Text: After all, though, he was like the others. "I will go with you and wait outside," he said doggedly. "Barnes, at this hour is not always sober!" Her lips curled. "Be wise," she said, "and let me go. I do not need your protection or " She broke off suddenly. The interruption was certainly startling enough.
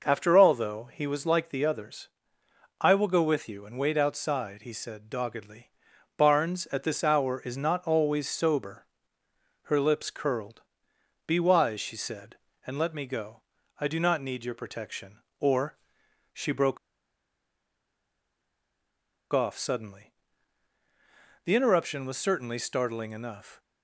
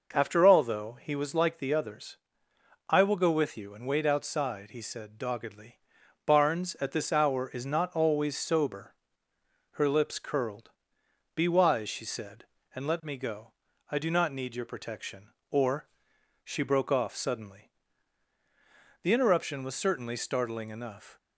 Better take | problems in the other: second | pauses between "broke" and "off"; strong; at 16.7 s; 2.5 s long

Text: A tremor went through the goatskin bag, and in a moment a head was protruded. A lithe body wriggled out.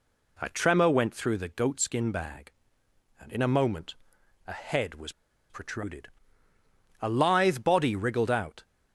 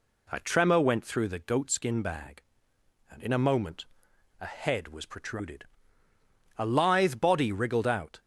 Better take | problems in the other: second | pauses between "moment" and "a"; noticeable; at 3.9 s; 0.50 s long; noticeable in the second // pauses between "was" and "protruded"; at 5.1 s; 0.38 s long

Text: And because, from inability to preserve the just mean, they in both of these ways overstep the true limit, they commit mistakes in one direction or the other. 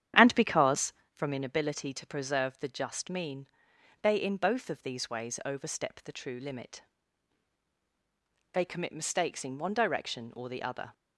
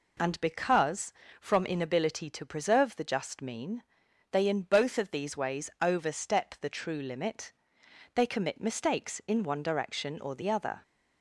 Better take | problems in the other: second | starts louder than the rest; strong; until 1.1 s; 10 dB

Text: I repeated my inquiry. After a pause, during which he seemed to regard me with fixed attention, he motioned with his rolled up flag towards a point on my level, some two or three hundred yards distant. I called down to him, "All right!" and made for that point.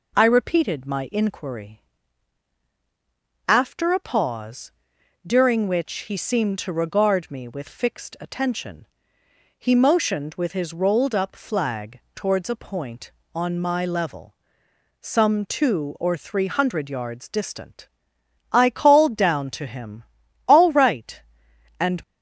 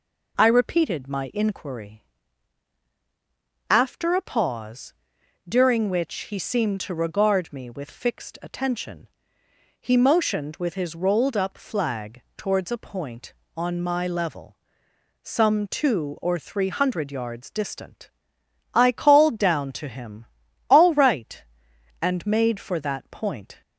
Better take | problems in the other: second | stops before "made for that point"; at 22.0 s

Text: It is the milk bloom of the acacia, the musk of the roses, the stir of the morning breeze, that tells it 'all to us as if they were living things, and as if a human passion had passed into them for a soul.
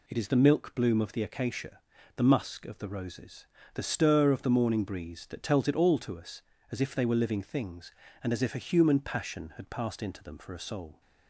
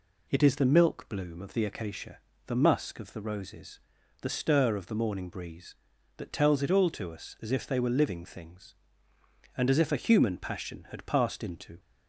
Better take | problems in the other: first | stops before "them for a soul"; at 11.7 s

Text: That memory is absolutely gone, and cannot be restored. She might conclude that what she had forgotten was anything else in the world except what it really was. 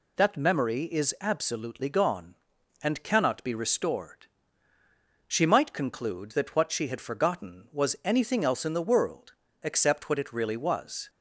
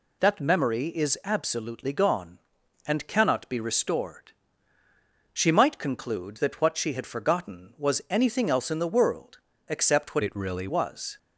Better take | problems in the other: first | pauses between "world" and "except"; slight; at 9.3 s; 0.32 s long; slight in the first // changes voice from "it" to "really"; from 10.2 to 10.6 s; 0.4 s long

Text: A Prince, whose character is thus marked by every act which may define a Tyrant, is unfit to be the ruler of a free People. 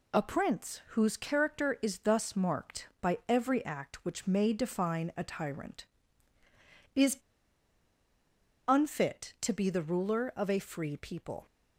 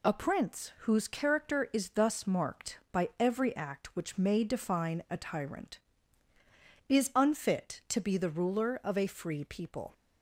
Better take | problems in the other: second | pauses between "is" and "unfit"; strong; at 7.1 s; 1.5 s long

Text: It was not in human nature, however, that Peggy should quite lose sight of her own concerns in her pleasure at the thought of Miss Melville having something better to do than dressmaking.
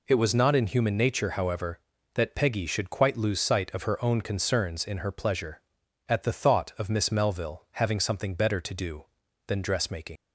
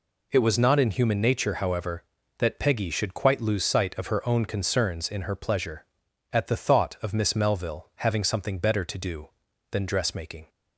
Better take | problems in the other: second | leaves "dressmaking" unfinished; at 10.1 s; 90 ms

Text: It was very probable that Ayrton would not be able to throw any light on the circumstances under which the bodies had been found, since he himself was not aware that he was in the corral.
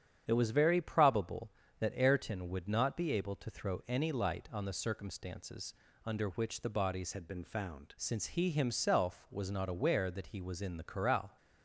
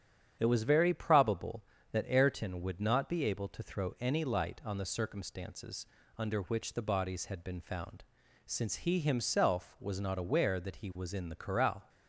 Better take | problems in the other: second | starts louder than the rest; strong; until 1.2 s; 8.5 dB; strong in the second // pauses between "circumstances" and "under"; slight; at 5.7 s; 0.32 s long; slight in the second // changes voice from "had" to "found"; from 7.1 to 7.9 s; 0.8 s long

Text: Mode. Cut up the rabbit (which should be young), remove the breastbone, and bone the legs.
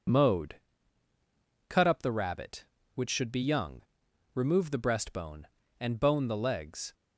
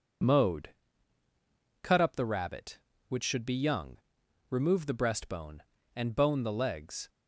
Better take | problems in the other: neither | none

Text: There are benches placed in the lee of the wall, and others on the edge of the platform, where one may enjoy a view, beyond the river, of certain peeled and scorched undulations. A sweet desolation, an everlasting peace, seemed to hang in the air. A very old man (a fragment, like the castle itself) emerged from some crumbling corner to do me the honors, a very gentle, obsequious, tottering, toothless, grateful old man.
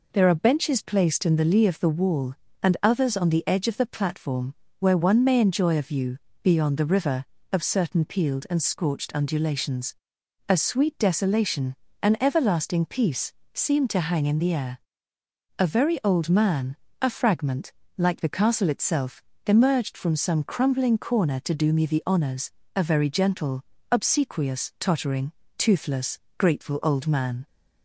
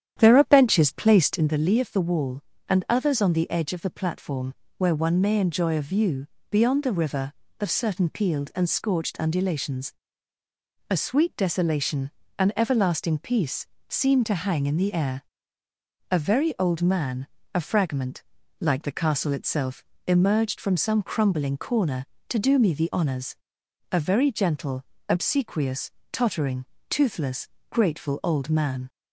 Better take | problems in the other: first | starts louder than the rest; strong; until 1.6 s; 10 dB

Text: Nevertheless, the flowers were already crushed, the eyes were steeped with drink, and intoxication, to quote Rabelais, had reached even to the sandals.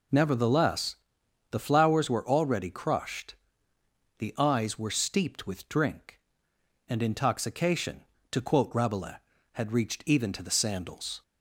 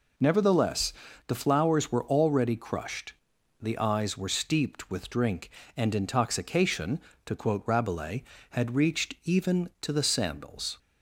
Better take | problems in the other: neither | none

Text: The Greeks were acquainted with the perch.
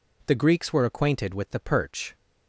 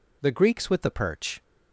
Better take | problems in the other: first | skips "were acquainted"; at 0.6 s

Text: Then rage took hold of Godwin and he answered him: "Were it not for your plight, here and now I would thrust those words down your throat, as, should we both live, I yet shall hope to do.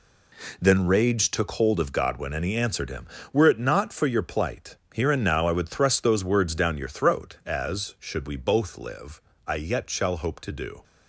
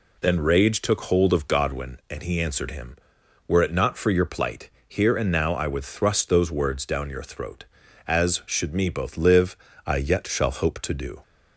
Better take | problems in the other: first | says "me" for "we"; at 8.7 s

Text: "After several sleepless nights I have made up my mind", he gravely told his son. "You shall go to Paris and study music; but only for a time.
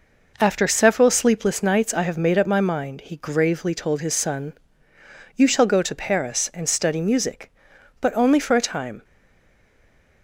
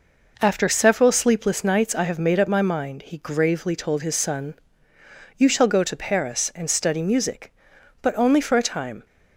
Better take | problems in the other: second | stays silent after the last word; noticeable; from 9.0 s on; 1.2 s long

